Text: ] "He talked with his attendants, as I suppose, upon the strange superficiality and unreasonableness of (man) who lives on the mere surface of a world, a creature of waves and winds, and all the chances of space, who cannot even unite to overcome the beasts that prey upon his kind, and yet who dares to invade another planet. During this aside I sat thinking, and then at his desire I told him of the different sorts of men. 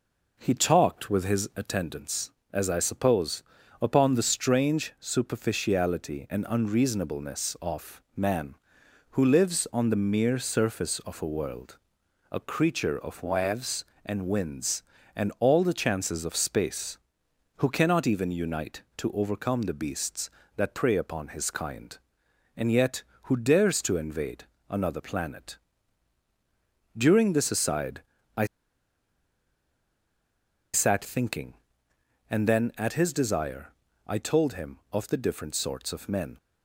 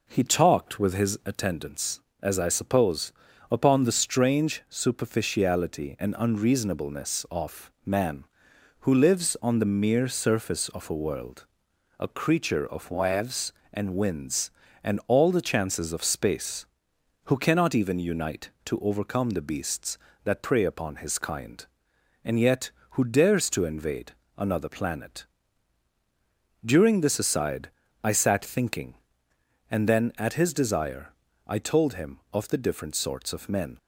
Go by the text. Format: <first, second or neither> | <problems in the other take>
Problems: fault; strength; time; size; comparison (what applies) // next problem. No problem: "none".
second | pauses between "invade" and "another"; slight; at 24.4 s; 0.24 s long; slight in the second // pauses between "aside" and "I"; slight; at 28.0 s; 0.34 s long; slight in the second // pauses between "I" and "sat"; strong; at 28.4 s; 2.2 s long // pauses between "desire" and "I"; slight; at 33.7 s; 0.34 s long; slight in the second